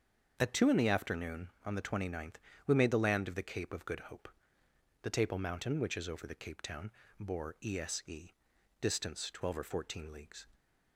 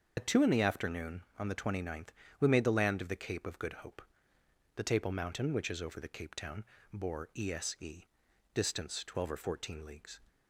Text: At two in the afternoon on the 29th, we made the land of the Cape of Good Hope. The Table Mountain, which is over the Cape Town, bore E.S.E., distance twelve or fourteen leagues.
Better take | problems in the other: first | loses the start of "At"; at 0.1 s; 45 ms // starts louder than the rest; until 1.1 s; 6.5 dB; also in the first

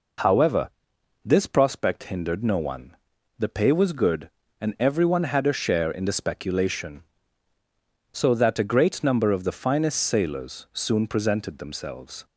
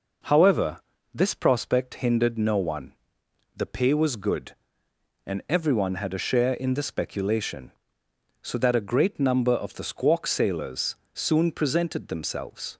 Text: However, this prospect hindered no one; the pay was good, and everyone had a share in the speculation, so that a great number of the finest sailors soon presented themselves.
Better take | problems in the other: first | says "squawk" for "finest"; at 9.8 s // pauses between "sailors" and "soon"; slight; at 10.9 s; 0.18 s long

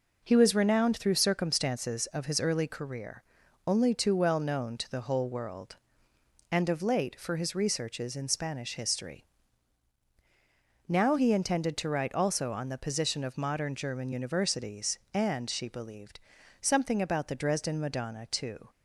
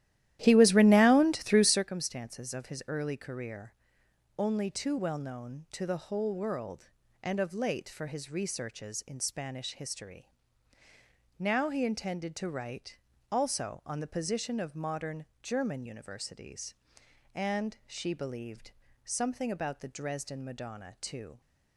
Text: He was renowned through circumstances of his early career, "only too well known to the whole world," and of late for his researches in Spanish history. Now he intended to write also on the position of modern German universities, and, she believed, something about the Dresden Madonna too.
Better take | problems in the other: first | starts louder than the rest; strong; until 1.9 s; 13.5 dB // pauses between "write" and "also"; slight; at 12.9 s; 0.30 s long // pauses between "modern" and "German"; slight; at 15.2 s; 0.18 s long

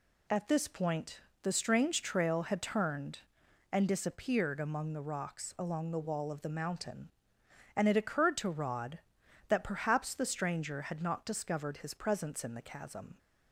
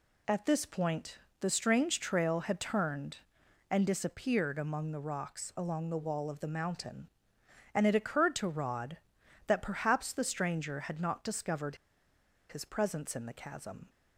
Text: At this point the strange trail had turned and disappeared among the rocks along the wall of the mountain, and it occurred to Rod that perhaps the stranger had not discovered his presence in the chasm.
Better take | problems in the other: first | pauses between "point" and "the"; slight; at 1.1 s; 0.22 s long; slight in the first // pauses between "discovered" and "his"; noticeable; at 11.7 s; 0.74 s long

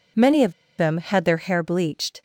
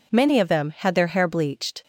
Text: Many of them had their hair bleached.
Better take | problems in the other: second | pauses between "of" and "them"; slight; at 0.5 s; 0.26 s long

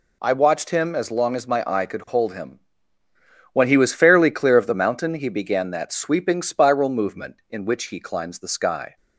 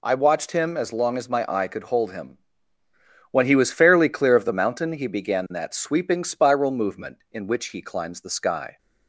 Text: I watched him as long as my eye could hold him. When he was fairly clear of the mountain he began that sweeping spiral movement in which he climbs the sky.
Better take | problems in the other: neither | none

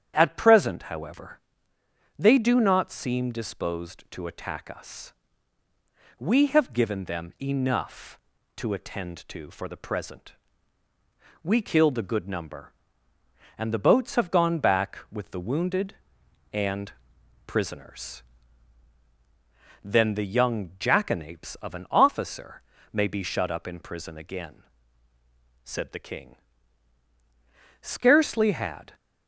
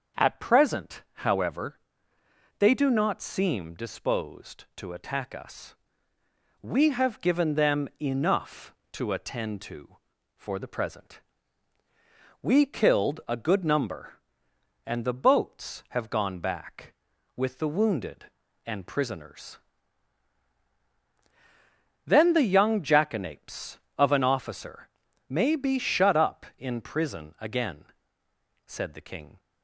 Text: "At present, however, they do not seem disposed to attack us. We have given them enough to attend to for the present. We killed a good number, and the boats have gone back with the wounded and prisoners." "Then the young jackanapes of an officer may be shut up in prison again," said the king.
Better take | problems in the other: second | starts louder than the rest; strong; until 1.1 s; 9.5 dB; also in the second // pauses between "and" and "prisoners"; noticeable; at 16.9 s; 0.52 s long // pauses between "officer" and "may"; slight; at 22.6 s; 0.30 s long; also in the second // goes on to say "Scarcely had"; noticeable; from 27.8 s on; 1.1 s long

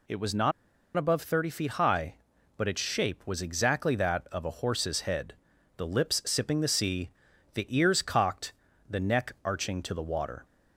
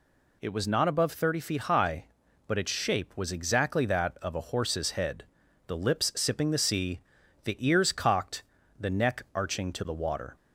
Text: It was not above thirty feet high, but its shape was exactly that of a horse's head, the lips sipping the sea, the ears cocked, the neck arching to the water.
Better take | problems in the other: second | pauses between "not" and "above"; at 0.5 s; 0.45 s long

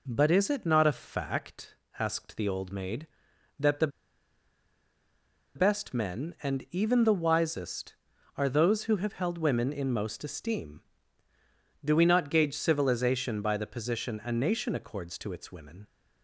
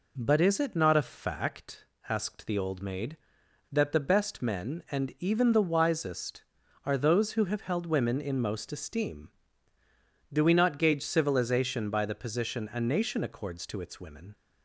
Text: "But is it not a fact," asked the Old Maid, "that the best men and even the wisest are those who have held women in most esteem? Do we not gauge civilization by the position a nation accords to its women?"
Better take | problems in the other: second | pauses between "the" and "best"; strong; at 3.8 s; 1.6 s long

